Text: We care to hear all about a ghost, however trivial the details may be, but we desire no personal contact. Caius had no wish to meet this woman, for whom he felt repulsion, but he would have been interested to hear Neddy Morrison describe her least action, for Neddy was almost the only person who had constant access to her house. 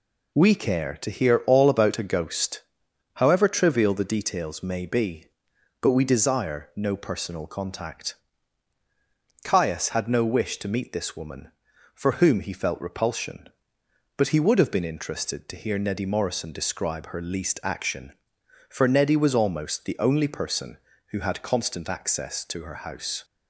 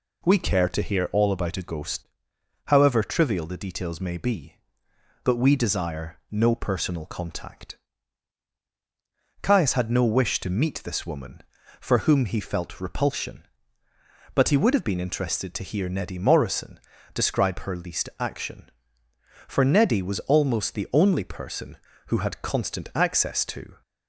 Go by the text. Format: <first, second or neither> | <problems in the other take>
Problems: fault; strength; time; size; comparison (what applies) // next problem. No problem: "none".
first | pauses between "Morrison" and "describe"; slight; at 16.7 s; 0.36 s long // stops before "her house"; at 23.8 s